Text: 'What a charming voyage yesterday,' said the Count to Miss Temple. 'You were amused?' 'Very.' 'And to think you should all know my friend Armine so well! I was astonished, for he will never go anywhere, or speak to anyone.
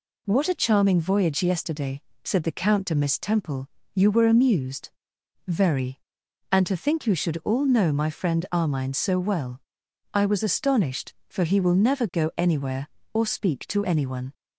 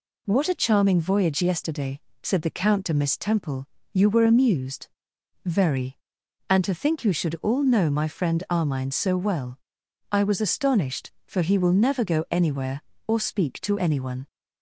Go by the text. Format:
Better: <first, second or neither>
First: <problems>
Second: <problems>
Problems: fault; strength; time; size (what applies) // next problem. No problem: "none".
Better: neither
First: none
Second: none